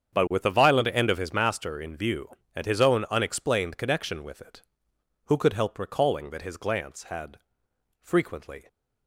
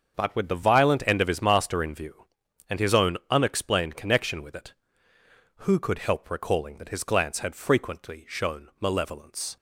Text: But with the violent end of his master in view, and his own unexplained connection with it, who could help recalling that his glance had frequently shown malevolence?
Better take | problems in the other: second | starts louder than the rest; strong; until 1.1 s; 7.5 dB; also in the second // pauses between "had" and "frequently"; noticeable; at 7.3 s; 0.64 s long // stops before "shown malevolence"; at 8.6 s

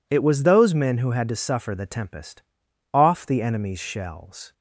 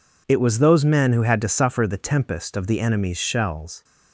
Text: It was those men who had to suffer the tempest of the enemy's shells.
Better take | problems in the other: second | says "off" for "of"; at 2.9 s

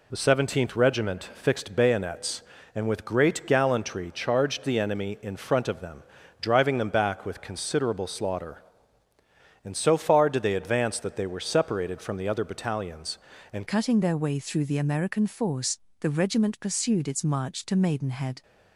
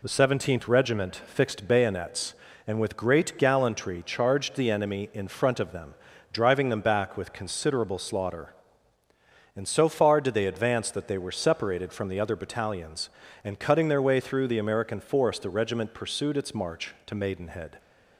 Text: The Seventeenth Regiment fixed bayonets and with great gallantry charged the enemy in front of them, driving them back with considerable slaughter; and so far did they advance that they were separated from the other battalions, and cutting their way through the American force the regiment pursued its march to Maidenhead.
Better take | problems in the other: second | changes voice at "cutting"; from 13.6 s on; 4.8 s long // pauses between "force" and "the"; slight; at 15.7 s; 0.22 s long

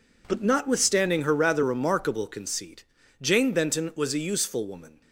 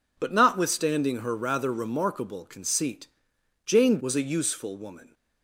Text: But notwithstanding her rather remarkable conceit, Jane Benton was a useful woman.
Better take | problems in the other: first | skips "Benton"; at 3.9 s

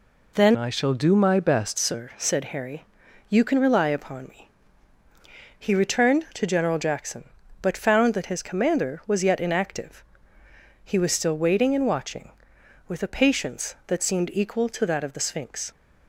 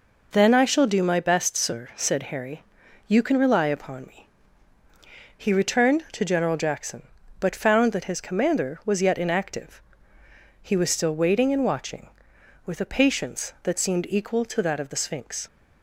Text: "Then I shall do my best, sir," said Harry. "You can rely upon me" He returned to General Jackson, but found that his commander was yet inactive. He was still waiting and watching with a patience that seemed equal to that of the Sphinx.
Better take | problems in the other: second | changes voice from "I" to "best"; from 0.5 to 1.7 s; 1.2 s long // pauses between "me" and "He"; at 4.4 s; 1.0 s long; also in the second

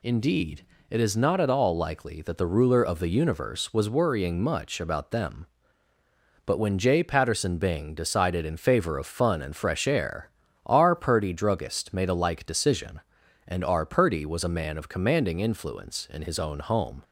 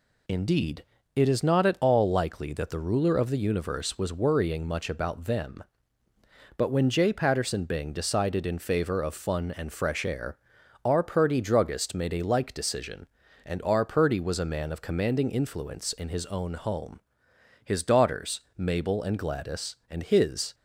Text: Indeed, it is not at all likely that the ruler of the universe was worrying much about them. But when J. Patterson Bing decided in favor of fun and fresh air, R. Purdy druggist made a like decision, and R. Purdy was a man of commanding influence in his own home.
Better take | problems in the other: first | goes on to say "His daughters Mabel and Gladys and his"; strong; from 17.6 s on; 2.9 s long

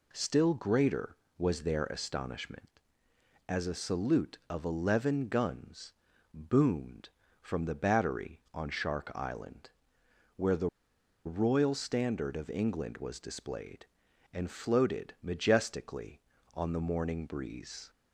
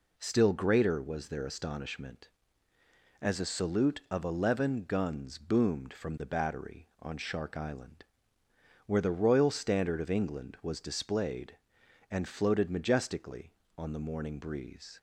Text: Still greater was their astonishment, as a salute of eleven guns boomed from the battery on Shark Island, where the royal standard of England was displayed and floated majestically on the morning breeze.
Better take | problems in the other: second | pauses between "guns" and "boomed"; at 5.9 s; 0.40 s long // pauses between "the" and "royal"; noticeable; at 10.6 s; 0.57 s long

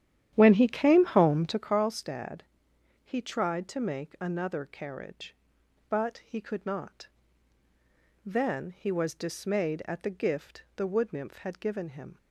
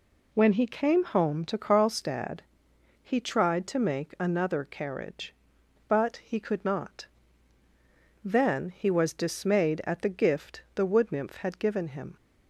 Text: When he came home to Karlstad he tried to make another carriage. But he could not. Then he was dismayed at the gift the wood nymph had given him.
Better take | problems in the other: second | starts louder than the rest; strong; until 1.7 s; 11 dB // pauses between "Karlstad" and "he"; noticeable; at 2.4 s; 0.64 s long; noticeable in the second

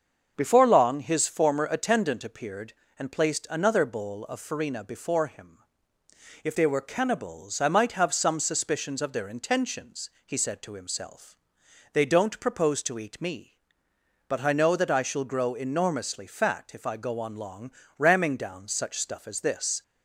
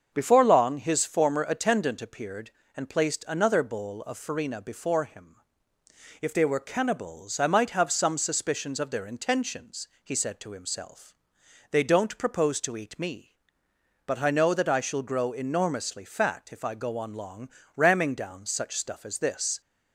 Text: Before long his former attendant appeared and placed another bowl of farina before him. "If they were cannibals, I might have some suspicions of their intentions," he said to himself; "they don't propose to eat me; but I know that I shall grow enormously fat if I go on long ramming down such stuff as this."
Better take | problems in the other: neither | starts louder than the rest; the same in both // pauses between "long" and "ramming"; slight; the same in both

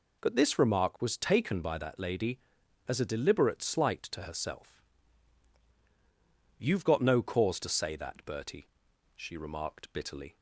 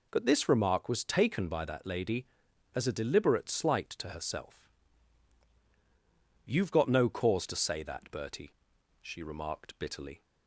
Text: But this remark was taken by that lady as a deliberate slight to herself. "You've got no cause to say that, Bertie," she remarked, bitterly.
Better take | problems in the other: neither | none

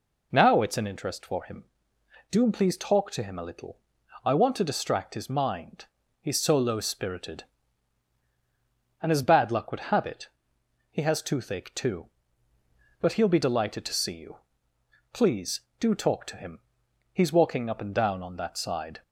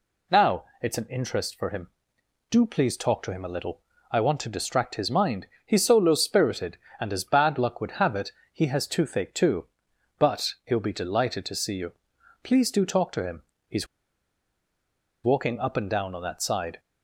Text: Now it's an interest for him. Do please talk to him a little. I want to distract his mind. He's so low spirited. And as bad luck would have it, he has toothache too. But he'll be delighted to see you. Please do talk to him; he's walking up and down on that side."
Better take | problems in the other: first | pauses between "Now" and "it's"; slight; at 0.6 s; 0.18 s long // pauses between "he's" and "walking"; strong; at 13.8 s; 1.3 s long

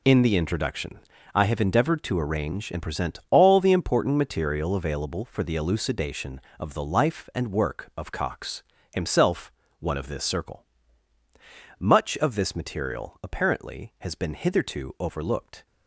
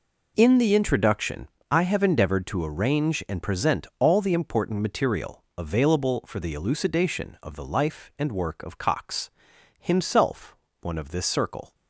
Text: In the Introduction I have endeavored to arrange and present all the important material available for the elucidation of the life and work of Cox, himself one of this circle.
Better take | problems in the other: second | pauses between "Introduction" and "I"; slight; at 0.9 s; 0.34 s long; slight in the second // pauses between "himself" and "one"; slight; at 9.5 s; 0.28 s long; slight in the second // goes on to say "Much of this material apparently has been hitherto overlooked"; strong; from 11.7 s on; 3.8 s long

